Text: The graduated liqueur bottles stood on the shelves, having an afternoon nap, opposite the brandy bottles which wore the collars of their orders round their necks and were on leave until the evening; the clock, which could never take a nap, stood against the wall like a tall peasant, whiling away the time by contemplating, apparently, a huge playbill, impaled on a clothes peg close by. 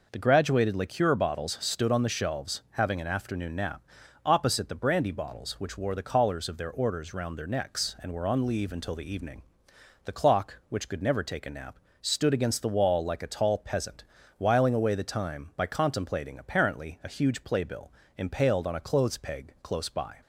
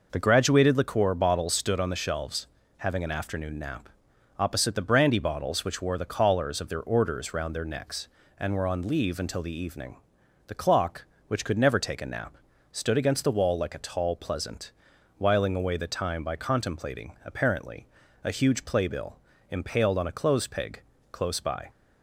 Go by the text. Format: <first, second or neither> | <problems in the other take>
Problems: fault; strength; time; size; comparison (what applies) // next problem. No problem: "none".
first | says "pleasant" for "peasant"; at 14.1 s // pauses between "peg" and "close"; slight; at 20.8 s; 0.32 s long